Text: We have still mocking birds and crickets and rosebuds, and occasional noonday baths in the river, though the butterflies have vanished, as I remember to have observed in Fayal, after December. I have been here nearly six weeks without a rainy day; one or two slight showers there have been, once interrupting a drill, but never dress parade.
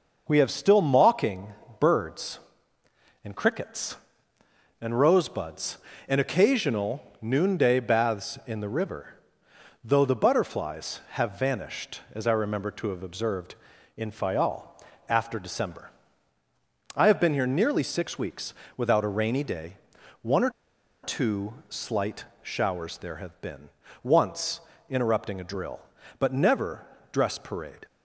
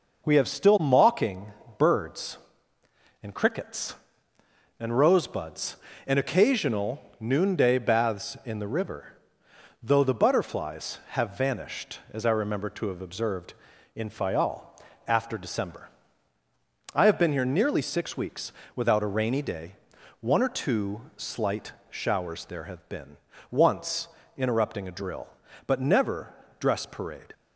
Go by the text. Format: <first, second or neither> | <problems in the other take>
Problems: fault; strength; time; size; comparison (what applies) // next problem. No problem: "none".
second | pauses between "mocking" and "birds"; slight; at 1.5 s; 0.26 s long; slight in the second // pauses between "occasional" and "noonday"; slight; at 7.0 s; 0.20 s long; slight in the second // pauses between "weeks" and "without"; slight; at 18.5 s; 0.24 s long; slight in the second // pauses between "or" and "two"; noticeable; at 20.5 s; 0.52 s long // pauses between "slight" and "showers"; slight; at 22.2 s; 0.18 s long; slight in the second // pauses between "once" and "interrupting"; slight; at 24.6 s; 0.28 s long; slight in the second // pauses between "never" and "dress"; slight; at 26.8 s; 0.26 s long; slight in the second